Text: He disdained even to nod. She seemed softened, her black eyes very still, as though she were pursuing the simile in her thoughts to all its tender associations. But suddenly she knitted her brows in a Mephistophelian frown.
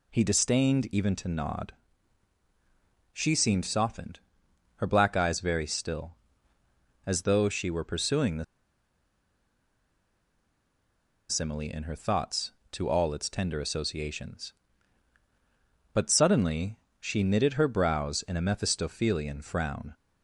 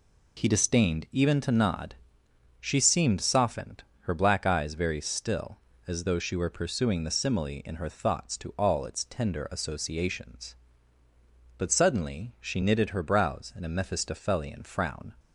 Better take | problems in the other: second | pauses between "the" and "simile"; strong; at 8.4 s; 2.8 s long // pauses between "suddenly" and "she"; slight; at 16.7 s; 0.22 s long

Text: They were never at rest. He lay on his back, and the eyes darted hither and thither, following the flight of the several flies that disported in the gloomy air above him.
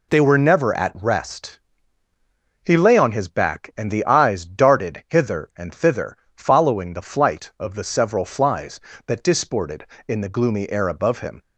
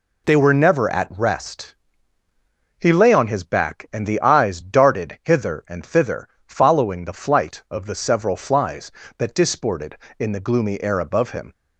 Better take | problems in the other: neither | none

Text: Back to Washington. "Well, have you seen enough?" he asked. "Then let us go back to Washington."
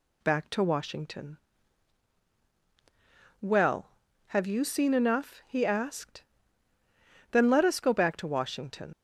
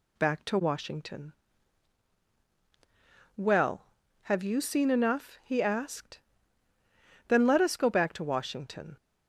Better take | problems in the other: second | leaves "Washington" unfinished; at 8.9 s; 65 ms

